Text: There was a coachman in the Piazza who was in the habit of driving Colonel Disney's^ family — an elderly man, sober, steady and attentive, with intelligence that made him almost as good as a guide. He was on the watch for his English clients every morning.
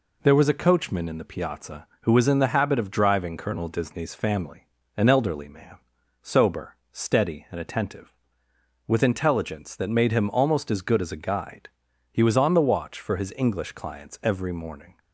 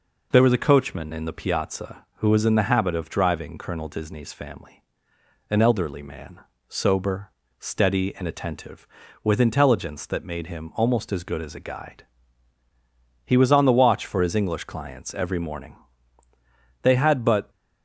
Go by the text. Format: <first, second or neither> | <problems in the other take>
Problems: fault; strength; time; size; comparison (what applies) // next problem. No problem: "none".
first | goes on to say "They had but"; noticeable; from 16.8 s on; 0.68 s long